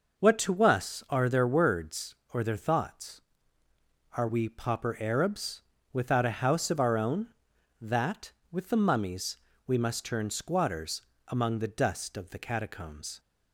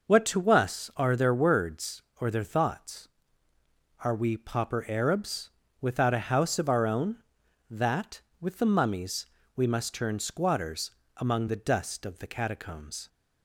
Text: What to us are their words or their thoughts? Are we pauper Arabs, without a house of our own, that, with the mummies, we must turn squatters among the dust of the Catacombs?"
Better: neither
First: pauses between "squatters" and "among"; slight; at 11.0 s; 0.26 s long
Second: pauses between "squatters" and "among"; slight; at 10.9 s; 0.26 s long

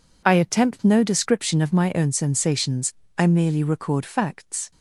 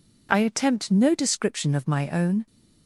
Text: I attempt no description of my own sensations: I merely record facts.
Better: first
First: none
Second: stops before "sensations I merely record facts"; at 2.4 s

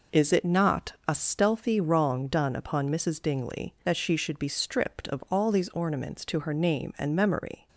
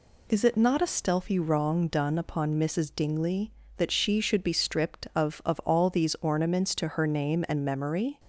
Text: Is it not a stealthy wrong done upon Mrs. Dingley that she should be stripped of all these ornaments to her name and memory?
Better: first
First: none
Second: says "of" twice; at 5.4 s

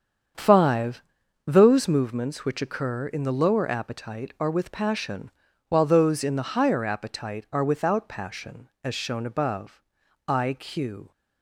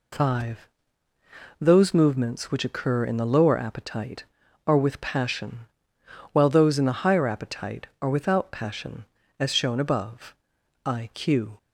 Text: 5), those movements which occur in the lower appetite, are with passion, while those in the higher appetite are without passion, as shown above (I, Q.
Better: second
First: starts louder than the rest; strong; until 2.0 s; 7.5 dB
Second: none

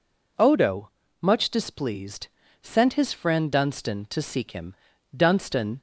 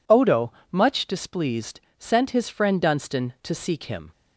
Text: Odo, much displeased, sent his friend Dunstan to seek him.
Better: second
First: goes on to say "Dunstan"; noticeable; from 5.1 s on; 0.64 s long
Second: none

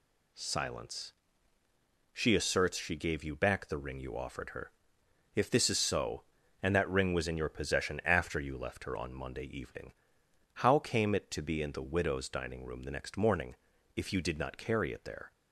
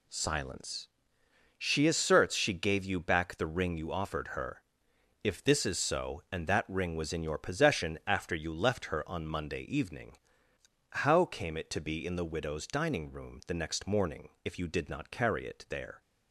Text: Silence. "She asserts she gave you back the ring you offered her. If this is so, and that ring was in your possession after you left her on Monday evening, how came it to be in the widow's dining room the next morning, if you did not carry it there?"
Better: neither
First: none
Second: none

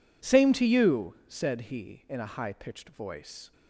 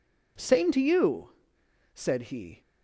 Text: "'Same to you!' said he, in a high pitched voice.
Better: first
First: none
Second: stops before "in a high pitched voice"; at 2.6 s

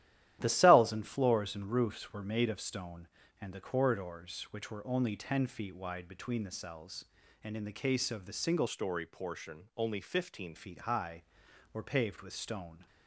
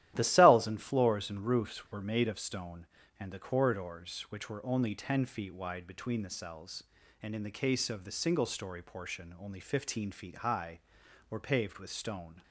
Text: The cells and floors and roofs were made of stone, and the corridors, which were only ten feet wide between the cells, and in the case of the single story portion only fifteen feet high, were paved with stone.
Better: second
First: starts louder than the rest; strong; until 1.4 s; 12.5 dB // changes voice from "story" to "fifteen"; from 8.6 to 10.5 s; 1.9 s long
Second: starts louder than the rest; strong; until 1.1 s; 13 dB

